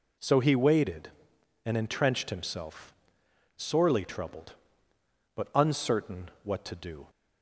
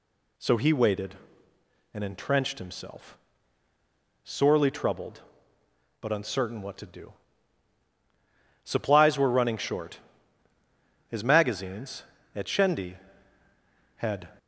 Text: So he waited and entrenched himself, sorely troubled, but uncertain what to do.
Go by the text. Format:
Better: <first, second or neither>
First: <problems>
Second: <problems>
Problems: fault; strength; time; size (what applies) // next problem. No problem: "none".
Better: first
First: none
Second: goes on to say "Supplies were running short His magazines at Shendi had"; strong; from 8.6 s on; 5.6 s long